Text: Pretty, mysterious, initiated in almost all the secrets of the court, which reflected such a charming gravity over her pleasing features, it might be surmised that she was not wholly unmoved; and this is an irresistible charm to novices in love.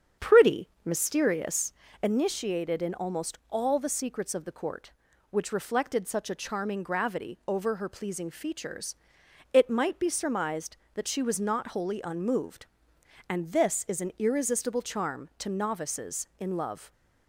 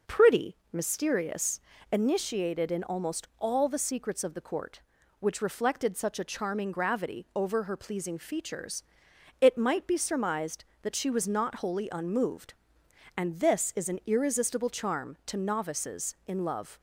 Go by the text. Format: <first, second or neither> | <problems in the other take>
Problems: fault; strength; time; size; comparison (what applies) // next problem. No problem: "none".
second | starts louder than the rest; strong; until 1.6 s; 7.5 dB